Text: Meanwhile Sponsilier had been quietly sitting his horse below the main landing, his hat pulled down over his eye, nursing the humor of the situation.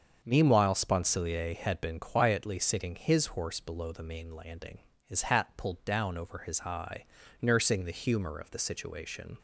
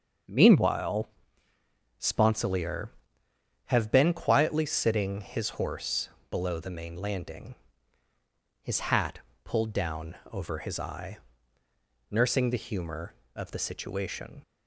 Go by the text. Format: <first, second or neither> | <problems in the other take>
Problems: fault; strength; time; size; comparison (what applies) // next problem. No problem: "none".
first | starts louder than the rest; until 2.2 s; 6.5 dB; also in the first // pauses between "Meanwhile" and "Sponsilier"; noticeable; at 1.0 s; 0.92 s long // says "have" for "had"; at 3.6 s // pauses between "horse" and "below"; slight; at 6.0 s; 0.22 s long // pauses between "hat" and "pulled"; slight; at 9.1 s; 0.24 s long // pauses between "down" and "over"; slight; at 10.1 s; 0.16 s long